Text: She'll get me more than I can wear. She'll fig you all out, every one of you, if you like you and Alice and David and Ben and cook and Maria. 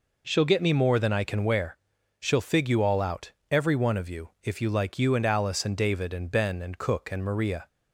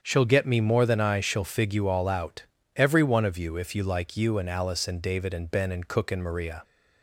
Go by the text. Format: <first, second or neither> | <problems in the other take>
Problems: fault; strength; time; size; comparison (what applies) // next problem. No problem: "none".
first | starts louder than the rest; strong; until 1.0 s; 7.5 dB // skips "can wear"; at 1.1 s